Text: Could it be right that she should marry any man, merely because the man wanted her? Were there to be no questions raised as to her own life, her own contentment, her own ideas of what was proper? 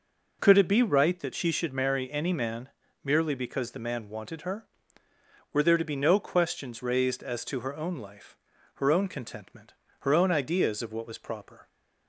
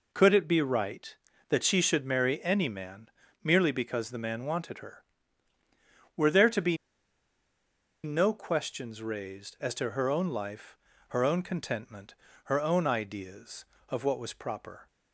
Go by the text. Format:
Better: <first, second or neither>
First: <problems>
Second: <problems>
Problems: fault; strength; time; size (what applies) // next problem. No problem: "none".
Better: first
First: none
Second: pauses between "be" and "no"; strong; at 6.7 s; 1.2 s long